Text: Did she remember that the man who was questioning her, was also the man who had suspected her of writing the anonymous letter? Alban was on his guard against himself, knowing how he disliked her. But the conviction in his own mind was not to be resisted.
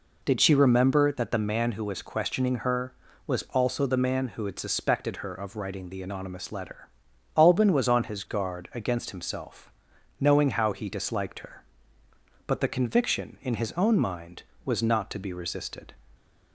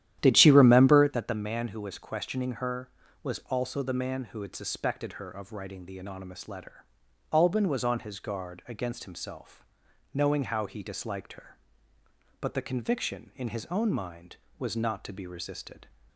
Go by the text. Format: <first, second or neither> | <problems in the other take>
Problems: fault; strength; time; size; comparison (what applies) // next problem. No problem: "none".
first | starts louder than the rest; strong; until 1.3 s; 11.5 dB